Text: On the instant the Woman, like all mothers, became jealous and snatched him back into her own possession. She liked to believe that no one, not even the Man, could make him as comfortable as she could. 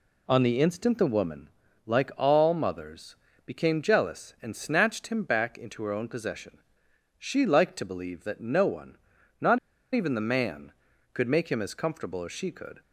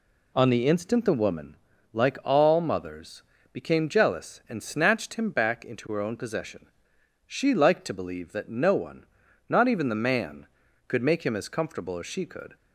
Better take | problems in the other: second | pauses between "not" and "even"; at 9.5 s; 0.36 s long

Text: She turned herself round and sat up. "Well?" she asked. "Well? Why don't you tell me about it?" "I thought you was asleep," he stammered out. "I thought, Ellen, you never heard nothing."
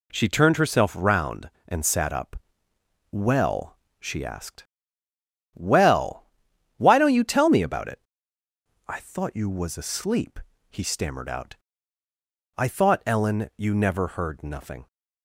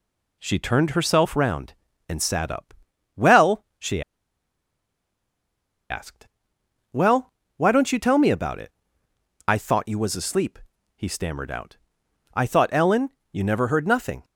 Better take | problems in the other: first | pauses between "she" and "asked"; strong; at 4.0 s; 1.8 s long

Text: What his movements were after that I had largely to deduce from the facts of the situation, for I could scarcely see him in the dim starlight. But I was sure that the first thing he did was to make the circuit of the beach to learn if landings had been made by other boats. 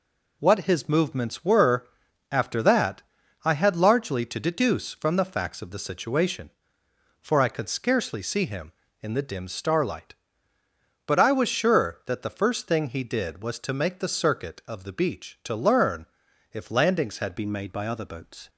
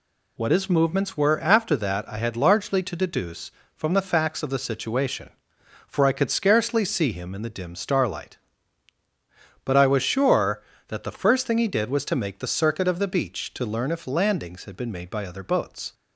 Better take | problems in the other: second | pauses between "were" and "after"; noticeable; at 1.8 s; 0.46 s long // pauses between "that" and "I"; at 3.0 s; 0.42 s long // pauses between "learn" and "if"; noticeable; at 16.0 s; 0.46 s long // changes voice at "been"; from 17.3 s on; 1.1 s long

